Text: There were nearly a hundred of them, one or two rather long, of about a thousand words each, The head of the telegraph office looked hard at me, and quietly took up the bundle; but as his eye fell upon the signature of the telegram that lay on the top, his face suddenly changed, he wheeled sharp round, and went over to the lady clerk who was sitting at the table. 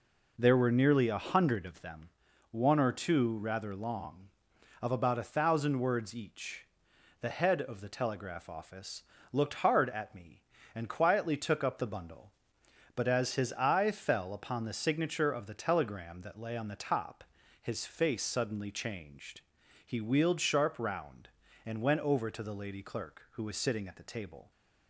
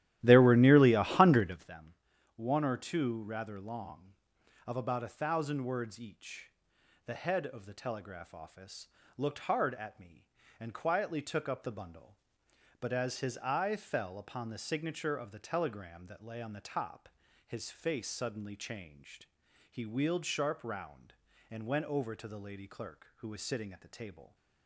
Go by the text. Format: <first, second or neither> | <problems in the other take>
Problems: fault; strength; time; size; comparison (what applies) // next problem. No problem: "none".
first | starts louder than the rest; strong; until 1.7 s; 14 dB // pauses between "office" and "looked"; slight; at 8.8 s; 0.30 s long; slight in the first